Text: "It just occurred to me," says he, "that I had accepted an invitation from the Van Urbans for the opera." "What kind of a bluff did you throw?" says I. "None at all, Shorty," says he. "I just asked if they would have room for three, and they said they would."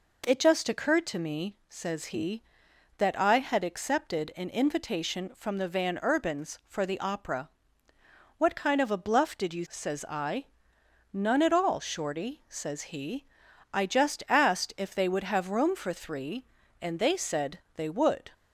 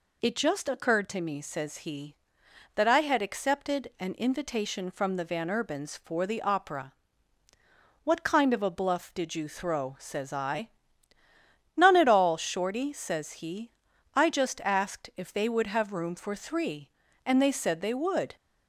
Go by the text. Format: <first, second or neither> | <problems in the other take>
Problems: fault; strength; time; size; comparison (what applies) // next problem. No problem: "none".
second | skips "throw"; at 9.6 s // pauses between "said" and "they"; slight; at 17.5 s; 0.16 s long